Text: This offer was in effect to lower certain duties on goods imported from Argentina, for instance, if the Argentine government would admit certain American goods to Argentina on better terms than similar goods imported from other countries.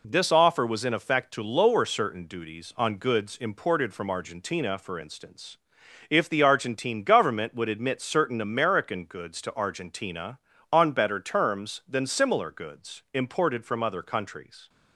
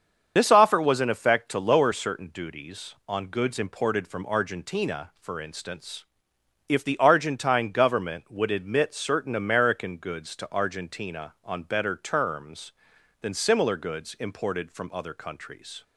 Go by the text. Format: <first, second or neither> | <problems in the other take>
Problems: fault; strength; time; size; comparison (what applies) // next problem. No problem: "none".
first | loses the start of "This"; at 0.3 s; 55 ms // starts louder than the rest; until 1.3 s; 7 dB